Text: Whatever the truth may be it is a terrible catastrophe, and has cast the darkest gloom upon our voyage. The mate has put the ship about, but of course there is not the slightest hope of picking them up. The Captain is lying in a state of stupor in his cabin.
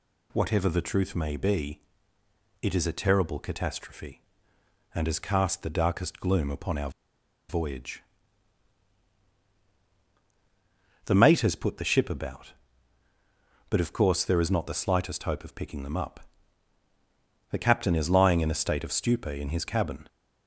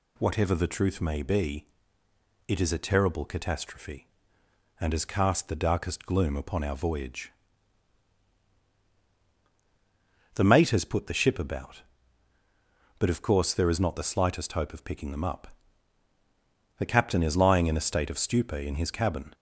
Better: second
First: pauses between "be" and "it"; noticeable; at 1.7 s; 0.82 s long // pauses between "our" and "voyage"; noticeable; at 6.8 s; 0.58 s long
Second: pauses between "be" and "it"; noticeable; at 1.6 s; 0.82 s long

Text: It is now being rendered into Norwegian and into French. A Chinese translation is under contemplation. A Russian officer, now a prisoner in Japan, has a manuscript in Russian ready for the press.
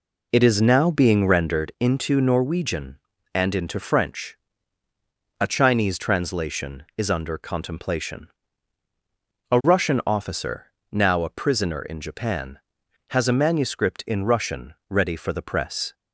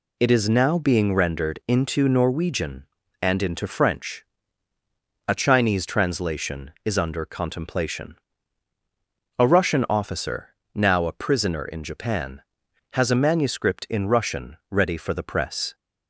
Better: second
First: starts louder than the rest; until 1.7 s; 3.5 dB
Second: none

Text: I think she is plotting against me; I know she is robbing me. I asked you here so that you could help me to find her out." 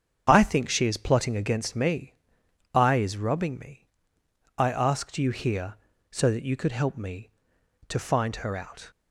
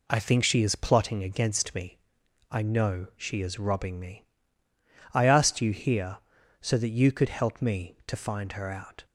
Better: second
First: starts louder than the rest; strong; until 1.2 s; 8 dB // skips "know she"; at 2.9 s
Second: none

